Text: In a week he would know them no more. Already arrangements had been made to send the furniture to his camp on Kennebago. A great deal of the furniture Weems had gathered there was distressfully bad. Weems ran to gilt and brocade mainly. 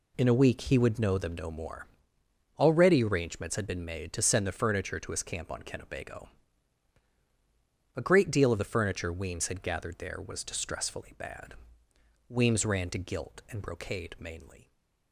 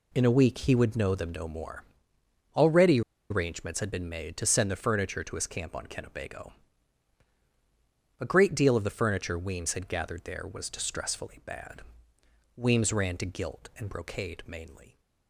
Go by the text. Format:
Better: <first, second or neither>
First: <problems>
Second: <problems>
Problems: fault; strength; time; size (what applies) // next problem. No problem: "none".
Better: first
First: none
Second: pauses between "Already" and "arrangements"; slight; at 3.0 s; 0.29 s long